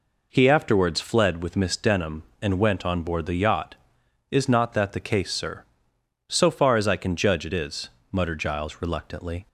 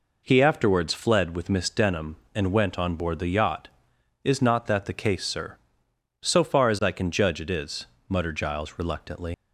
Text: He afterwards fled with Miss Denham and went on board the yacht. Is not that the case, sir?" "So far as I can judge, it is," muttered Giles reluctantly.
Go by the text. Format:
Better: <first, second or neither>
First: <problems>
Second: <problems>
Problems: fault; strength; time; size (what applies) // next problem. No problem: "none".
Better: first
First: none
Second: leaves "reluctantly" unfinished; at 9.3 s; 100 ms